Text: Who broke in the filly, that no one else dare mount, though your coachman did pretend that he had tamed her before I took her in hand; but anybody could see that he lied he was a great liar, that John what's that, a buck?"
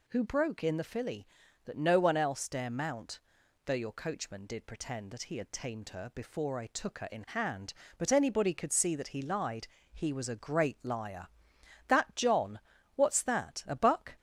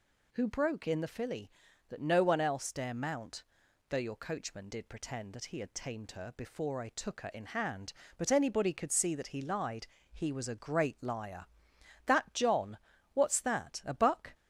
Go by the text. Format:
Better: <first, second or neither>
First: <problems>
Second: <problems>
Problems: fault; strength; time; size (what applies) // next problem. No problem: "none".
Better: neither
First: pauses between "lied" and "he"; slight; at 9.6 s; 0.26 s long // pauses between "John" and "what's"; slight; at 12.6 s; 0.34 s long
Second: pauses between "lied" and "he"; slight; at 9.8 s; 0.26 s long // pauses between "John" and "what's"; slight; at 12.7 s; 0.34 s long